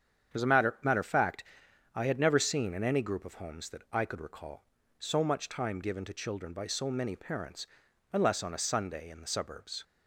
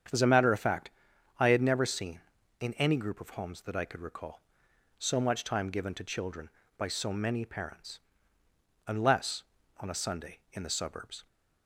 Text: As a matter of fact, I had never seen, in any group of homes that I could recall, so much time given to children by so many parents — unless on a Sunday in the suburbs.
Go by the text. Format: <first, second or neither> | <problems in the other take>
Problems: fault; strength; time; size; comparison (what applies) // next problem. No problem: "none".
second | starts louder than the rest; strong; until 1.3 s; 8 dB; strong in the second // says "matter" twice; at 0.8 s